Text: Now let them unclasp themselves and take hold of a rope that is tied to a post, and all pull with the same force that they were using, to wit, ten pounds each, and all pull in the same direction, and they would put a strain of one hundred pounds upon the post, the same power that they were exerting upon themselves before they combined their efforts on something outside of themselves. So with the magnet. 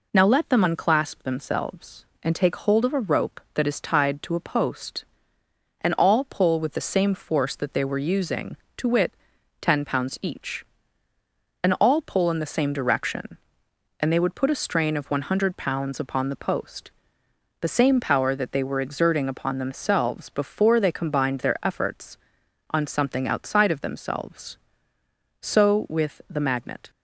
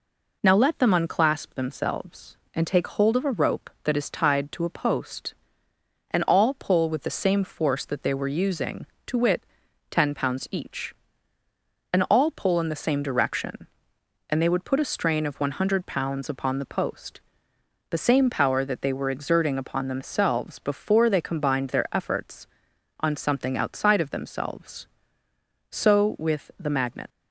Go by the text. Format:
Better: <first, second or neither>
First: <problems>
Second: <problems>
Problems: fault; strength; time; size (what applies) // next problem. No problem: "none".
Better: first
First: none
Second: leaves "magnet" unfinished; at 27.1 s; 90 ms